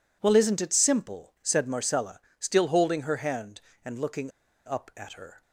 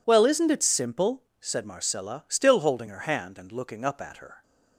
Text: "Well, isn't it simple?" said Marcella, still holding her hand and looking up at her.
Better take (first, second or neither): second